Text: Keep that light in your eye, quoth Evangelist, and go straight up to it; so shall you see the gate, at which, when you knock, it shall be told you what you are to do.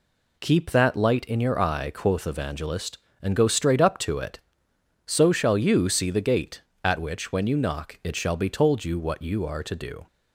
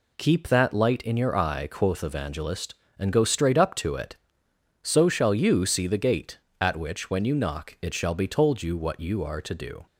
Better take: neither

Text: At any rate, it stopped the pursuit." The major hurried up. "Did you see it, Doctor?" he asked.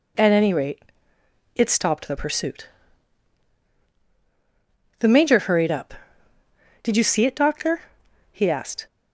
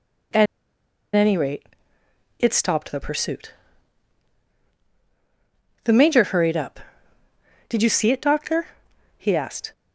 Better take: first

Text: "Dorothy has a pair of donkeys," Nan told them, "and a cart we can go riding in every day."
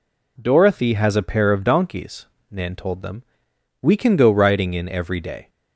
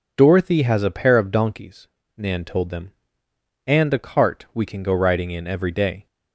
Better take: second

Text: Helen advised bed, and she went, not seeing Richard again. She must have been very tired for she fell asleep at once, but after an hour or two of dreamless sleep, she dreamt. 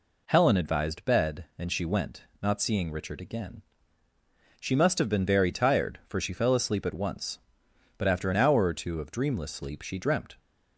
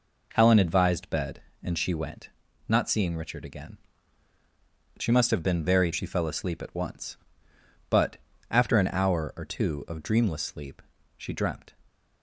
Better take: first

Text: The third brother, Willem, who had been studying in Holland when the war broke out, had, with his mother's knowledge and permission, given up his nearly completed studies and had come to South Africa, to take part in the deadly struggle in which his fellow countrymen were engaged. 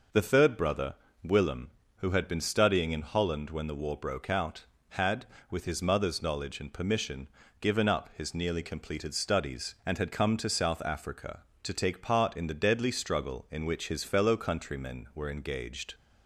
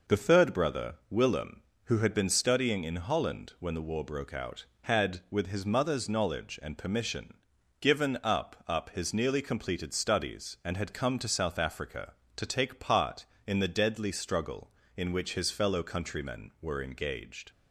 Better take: first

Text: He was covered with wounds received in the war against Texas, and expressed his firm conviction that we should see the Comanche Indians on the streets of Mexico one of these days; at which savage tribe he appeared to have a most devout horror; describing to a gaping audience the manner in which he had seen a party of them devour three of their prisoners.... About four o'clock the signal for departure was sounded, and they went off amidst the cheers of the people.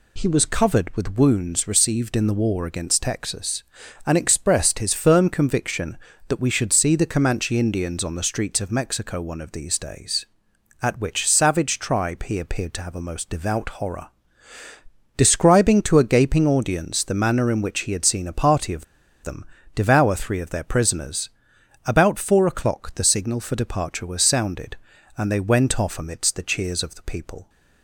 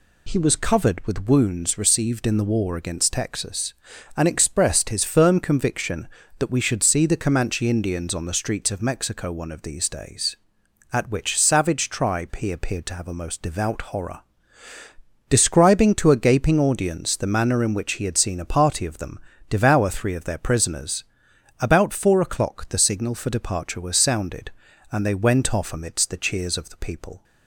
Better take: second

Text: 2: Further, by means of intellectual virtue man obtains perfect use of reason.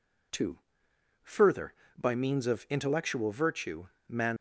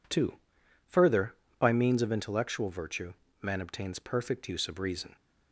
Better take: second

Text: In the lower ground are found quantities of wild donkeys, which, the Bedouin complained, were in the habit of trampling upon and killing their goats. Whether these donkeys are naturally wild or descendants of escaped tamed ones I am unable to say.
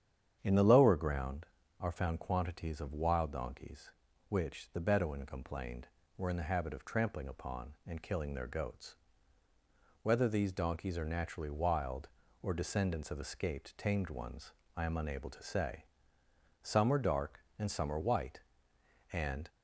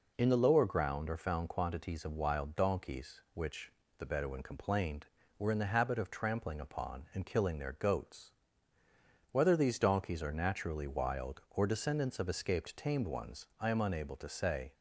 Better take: second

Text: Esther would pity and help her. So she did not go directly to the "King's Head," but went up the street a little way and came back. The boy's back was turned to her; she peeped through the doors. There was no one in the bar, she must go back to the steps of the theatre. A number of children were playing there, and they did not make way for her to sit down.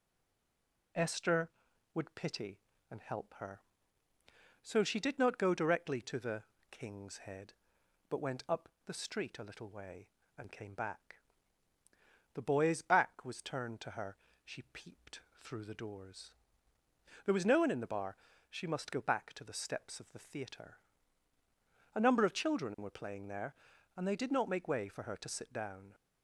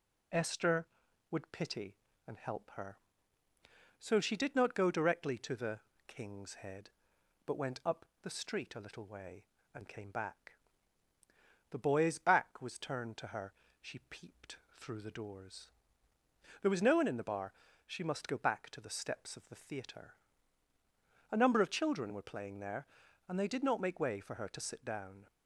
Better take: second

